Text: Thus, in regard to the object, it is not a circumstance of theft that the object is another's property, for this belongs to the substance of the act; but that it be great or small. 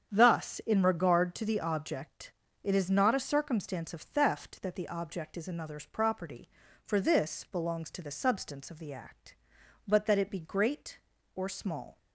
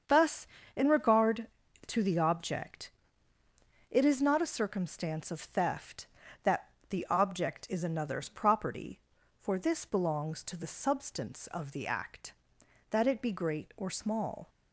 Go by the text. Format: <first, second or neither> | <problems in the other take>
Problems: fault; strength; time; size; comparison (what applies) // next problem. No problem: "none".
first | starts louder than the rest; strong; until 1.3 s; 7 dB; strong in the first // pauses between "that" and "the"; slight; at 6.6 s; 0.24 s long // skips "but"; at 12.6 s